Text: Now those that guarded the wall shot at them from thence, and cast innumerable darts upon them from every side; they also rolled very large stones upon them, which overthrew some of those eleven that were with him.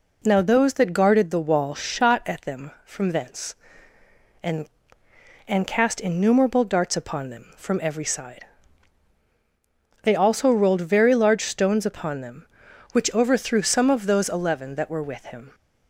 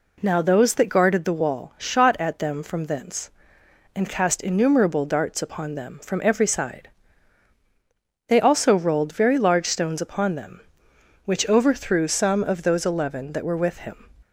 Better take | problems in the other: second | says "and" twice; at 5.4 s

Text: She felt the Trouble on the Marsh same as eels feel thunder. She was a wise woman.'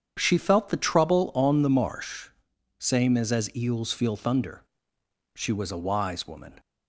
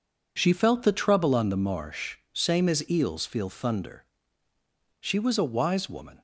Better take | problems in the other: second | starts louder than the rest; strong; until 1.1 s; 8 dB // pauses between "Marsh" and "same"; noticeable; at 2.2 s; 0.50 s long // says "as" twice; at 3.3 s

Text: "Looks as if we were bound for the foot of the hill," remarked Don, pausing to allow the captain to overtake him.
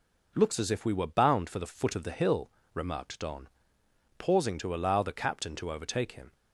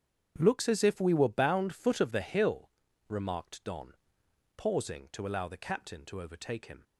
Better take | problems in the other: first | starts louder than the rest; strong; until 1.3 s; 8.5 dB // skips "for the"; at 1.7 s

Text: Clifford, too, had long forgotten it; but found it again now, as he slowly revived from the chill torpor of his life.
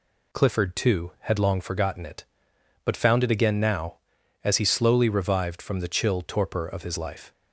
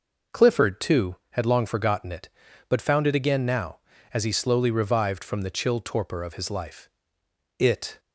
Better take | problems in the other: first | goes on to say "It"; slight; from 7.5 s on; 0.40 s long

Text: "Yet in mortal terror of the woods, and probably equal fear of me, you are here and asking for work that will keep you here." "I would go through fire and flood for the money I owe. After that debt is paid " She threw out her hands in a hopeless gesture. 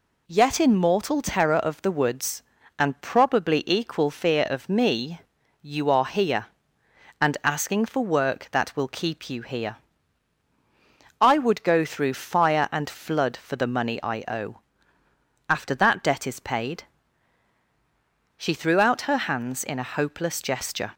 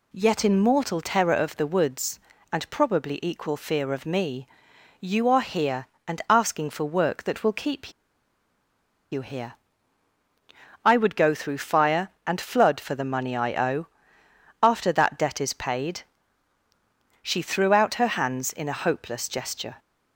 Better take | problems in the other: first | pauses between "keep" and "you"; at 7.9 s; 1.2 s long

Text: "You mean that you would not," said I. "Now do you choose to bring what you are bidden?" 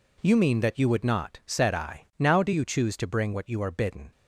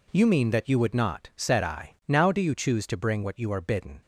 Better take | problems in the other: neither | none

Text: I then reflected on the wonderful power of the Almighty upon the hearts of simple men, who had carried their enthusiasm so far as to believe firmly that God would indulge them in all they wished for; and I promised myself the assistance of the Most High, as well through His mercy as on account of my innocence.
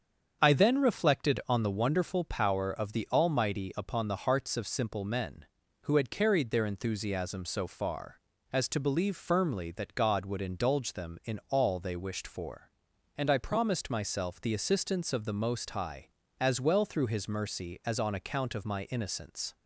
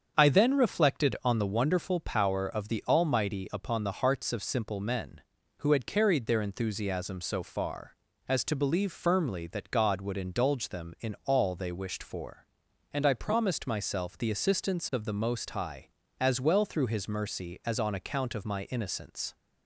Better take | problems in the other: neither | starts louder than the rest; strong; the same in both

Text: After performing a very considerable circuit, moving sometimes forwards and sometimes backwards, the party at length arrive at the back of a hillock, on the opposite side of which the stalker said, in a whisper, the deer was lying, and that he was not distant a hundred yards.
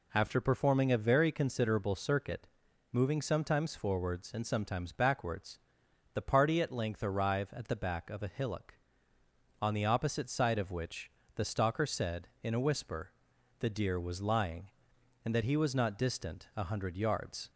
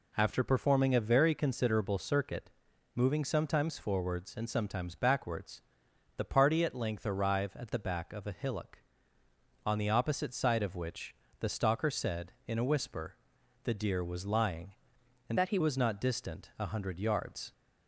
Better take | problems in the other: first | pauses between "which" and "the"; slight; at 11.1 s; 0.26 s long; slight in the first // changes voice from "that" to "he"; from 15.3 to 15.5 s; 0.2 s long

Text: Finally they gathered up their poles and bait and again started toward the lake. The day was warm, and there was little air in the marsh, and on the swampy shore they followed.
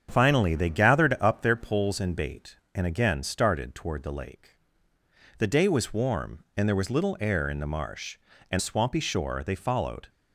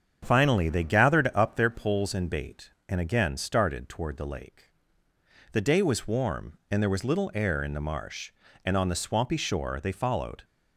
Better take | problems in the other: second | starts louder than the rest; strong; until 1.1 s; 8 dB; strong in the second // skips "on the"; at 8.5 s

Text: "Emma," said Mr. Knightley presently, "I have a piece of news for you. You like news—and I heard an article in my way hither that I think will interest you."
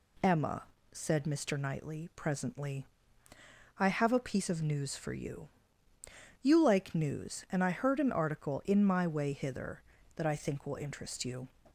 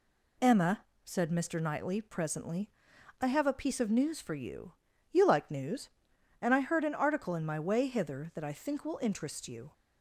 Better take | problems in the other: neither | none

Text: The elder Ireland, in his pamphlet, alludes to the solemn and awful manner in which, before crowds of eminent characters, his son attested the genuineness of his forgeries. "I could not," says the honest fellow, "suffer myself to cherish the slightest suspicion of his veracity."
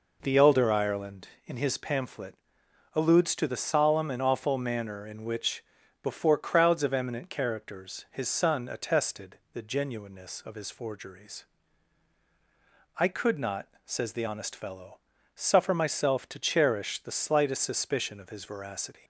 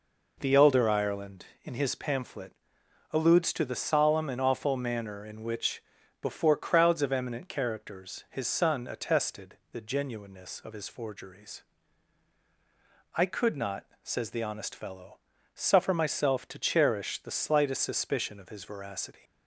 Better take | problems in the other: neither | pauses between "attested" and "the"; slight; the same in both

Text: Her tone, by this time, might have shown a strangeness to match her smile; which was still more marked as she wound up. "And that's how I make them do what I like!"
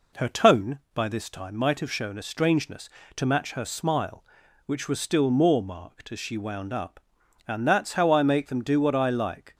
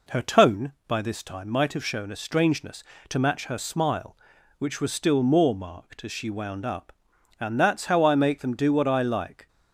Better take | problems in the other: neither | none

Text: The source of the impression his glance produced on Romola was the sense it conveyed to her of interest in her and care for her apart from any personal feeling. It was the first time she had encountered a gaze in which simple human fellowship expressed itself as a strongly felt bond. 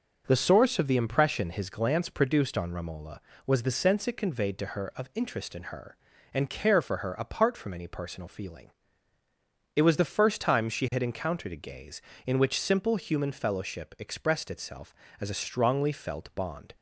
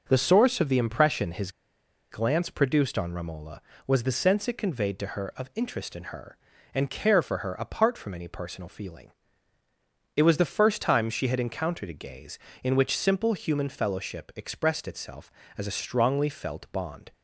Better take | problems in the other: first | pauses between "his" and "glance"; noticeable; at 1.5 s; 0.60 s long

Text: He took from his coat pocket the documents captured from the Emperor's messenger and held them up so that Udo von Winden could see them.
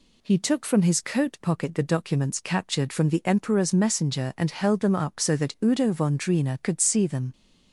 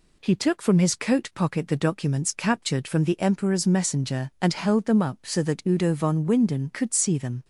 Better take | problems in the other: second | says "Drina" for "Winden"; at 6.1 s

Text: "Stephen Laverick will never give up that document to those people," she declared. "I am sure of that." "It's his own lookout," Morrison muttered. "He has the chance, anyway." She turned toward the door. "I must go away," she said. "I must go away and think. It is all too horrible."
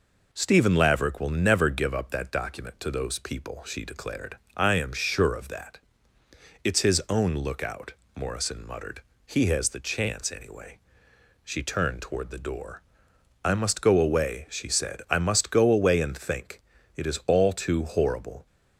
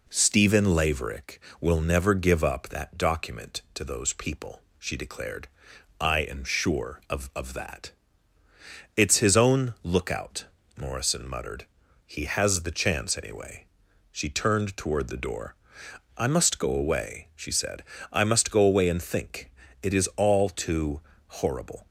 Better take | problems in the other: first | says "of" twice; at 7.3 s // pauses between "too" and "horrible"; slight; at 21.0 s; 0.26 s long

